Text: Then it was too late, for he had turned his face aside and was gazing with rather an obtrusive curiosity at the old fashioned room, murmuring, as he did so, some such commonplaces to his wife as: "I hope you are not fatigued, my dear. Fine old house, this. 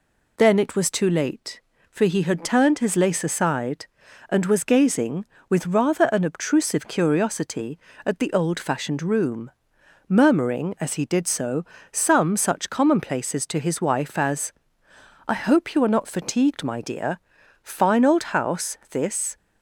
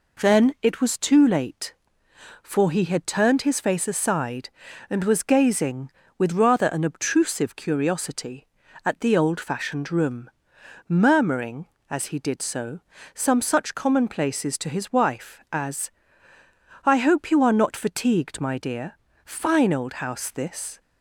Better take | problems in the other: second | says "lace" for "face"; at 2.9 s

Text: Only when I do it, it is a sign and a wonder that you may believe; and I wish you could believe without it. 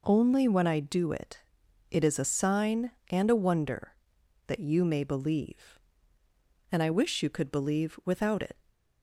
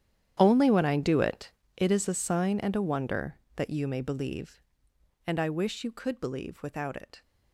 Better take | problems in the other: first | gets quieter; strong; throughout; 17 dB

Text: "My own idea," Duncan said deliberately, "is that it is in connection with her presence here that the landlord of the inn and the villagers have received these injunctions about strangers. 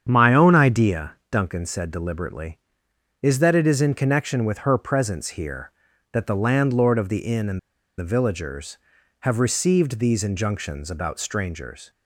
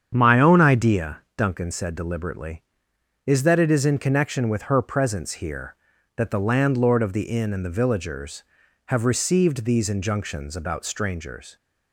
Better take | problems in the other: second | starts louder than the rest; strong; until 1.1 s; 8 dB; strong in the second // pauses between "and" and "the"; at 7.5 s; 0.38 s long

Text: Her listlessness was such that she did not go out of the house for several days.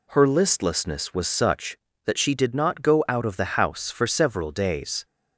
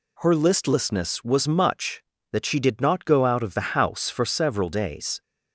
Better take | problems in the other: first | says "much" for "such"; at 1.4 s

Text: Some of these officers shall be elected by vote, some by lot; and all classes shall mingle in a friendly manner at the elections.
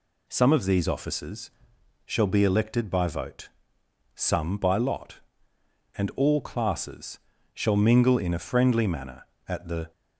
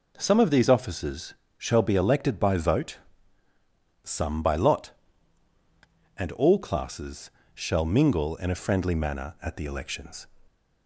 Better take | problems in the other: second | pauses between "officers" and "shall"; noticeable; at 1.5 s; 0.54 s long; slight in the second // pauses between "classes" and "shall"; slight; at 7.1 s; 0.34 s long; slight in the second // stops before "elections"; at 9.9 s

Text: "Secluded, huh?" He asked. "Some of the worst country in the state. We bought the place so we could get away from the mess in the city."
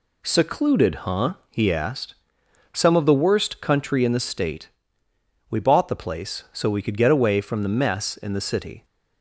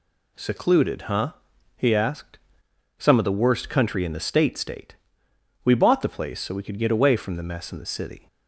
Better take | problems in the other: first | says "state" twice; at 4.5 s

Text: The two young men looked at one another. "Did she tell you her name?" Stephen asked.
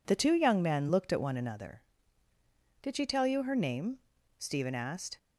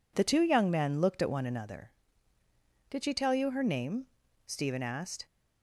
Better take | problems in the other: neither | none

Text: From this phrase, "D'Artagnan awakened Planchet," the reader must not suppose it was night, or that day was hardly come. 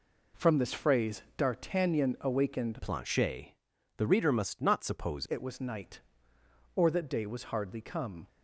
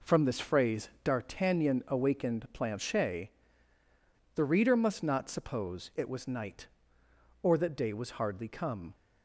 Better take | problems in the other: second | changes voice from "Planchet" to "suppose"; from 2.8 to 5.2 s; 2.4 s long

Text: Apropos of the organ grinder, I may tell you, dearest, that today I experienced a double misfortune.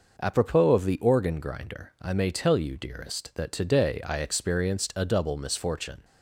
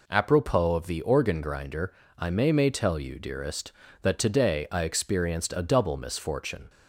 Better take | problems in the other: first | says "may" twice; at 2.5 s

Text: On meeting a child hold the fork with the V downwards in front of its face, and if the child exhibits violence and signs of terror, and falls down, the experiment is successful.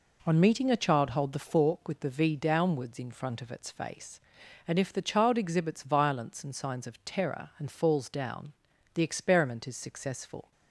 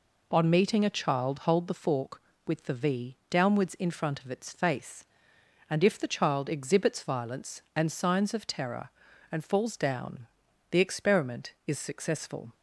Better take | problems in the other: neither | none

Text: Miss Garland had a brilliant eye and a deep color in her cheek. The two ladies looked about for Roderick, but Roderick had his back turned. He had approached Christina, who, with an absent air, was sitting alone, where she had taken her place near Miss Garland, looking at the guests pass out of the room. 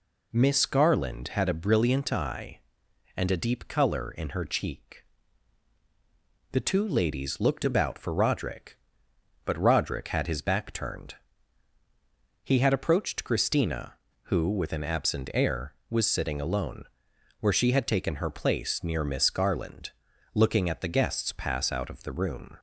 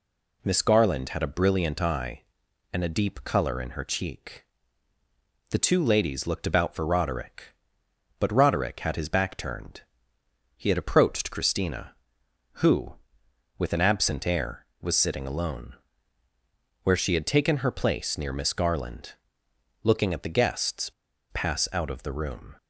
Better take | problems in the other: first | pauses between "guests" and "pass"; at 20.8 s; 0.43 s long

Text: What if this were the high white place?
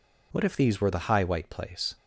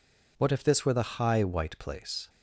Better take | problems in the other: second | says "these" for "this"; at 0.5 s

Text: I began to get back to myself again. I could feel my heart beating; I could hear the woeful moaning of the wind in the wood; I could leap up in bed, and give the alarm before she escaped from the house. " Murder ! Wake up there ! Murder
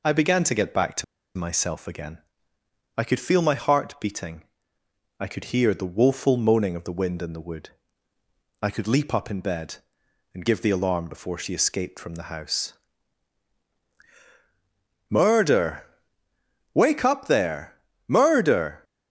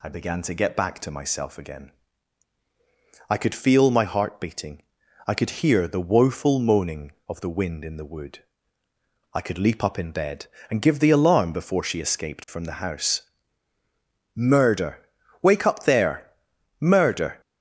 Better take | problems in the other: second | pauses between "to" and "myself"; slight; at 1.0 s; 0.32 s long

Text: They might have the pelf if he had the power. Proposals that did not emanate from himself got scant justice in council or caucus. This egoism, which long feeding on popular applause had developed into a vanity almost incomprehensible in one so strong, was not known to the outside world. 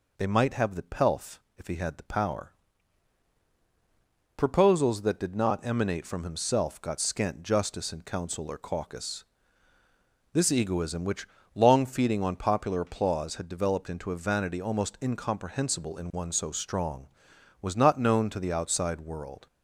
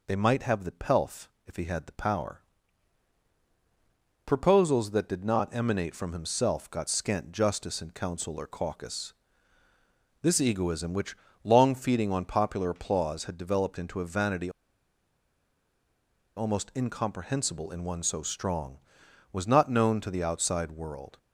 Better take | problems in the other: first | pauses between "pelf" and "if"; slight; at 1.2 s; 0.18 s long; slight in the first // pauses between "which" and "long"; slight; at 11.1 s; 0.26 s long; slight in the first // pauses between "vanity" and "almost"; strong; at 14.5 s; 1.8 s long

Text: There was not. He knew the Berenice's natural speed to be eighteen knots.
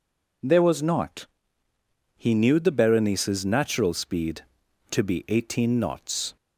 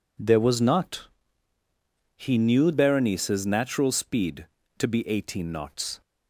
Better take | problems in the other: first | skips "the"; at 2.7 s

